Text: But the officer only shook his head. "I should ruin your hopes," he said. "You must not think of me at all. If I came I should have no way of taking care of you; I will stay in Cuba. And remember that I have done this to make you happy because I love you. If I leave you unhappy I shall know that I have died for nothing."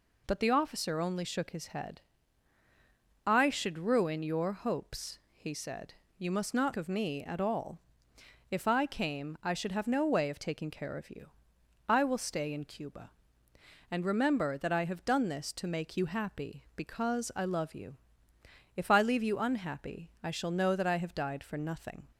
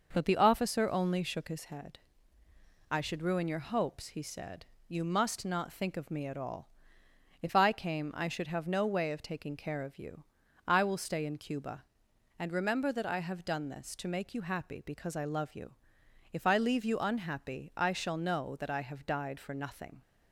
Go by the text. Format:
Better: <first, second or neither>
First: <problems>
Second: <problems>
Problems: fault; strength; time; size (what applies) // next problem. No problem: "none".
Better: second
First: skips "think"; at 6.7 s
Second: none